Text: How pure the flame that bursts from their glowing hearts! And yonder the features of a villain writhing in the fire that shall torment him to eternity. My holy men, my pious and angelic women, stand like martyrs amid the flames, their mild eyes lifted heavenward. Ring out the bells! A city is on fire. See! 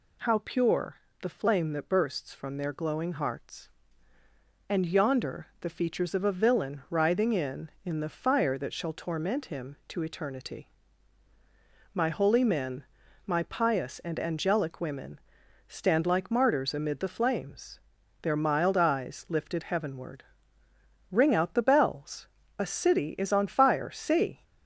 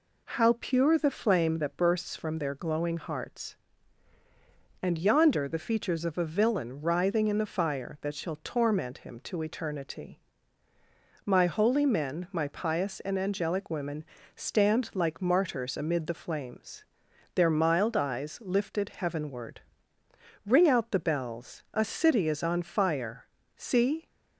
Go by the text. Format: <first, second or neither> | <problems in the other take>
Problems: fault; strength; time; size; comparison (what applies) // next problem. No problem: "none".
second | pauses between "pure" and "the"; slight; at 0.9 s; 0.24 s long // says "in" twice; at 7.8 s